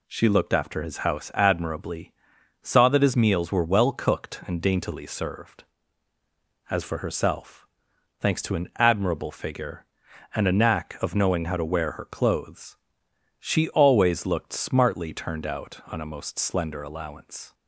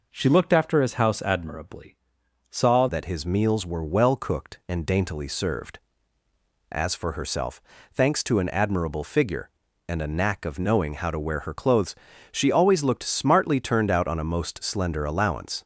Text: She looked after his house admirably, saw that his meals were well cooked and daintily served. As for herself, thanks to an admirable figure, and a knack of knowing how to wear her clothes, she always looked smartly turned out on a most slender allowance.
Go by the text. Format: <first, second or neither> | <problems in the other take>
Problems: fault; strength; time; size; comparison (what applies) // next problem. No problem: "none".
first | changes voice at "that"; from 2.8 s on; 12.8 s long